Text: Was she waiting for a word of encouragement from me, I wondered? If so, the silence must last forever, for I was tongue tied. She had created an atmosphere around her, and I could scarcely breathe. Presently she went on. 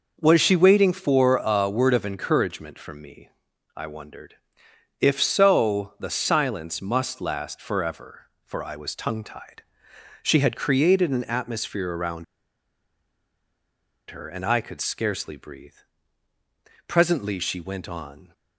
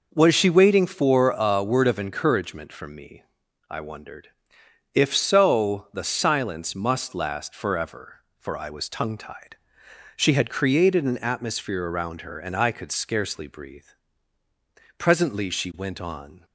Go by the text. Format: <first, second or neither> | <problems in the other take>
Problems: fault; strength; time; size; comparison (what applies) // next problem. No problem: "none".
second | pauses between "around" and "her"; strong; at 12.2 s; 1.8 s long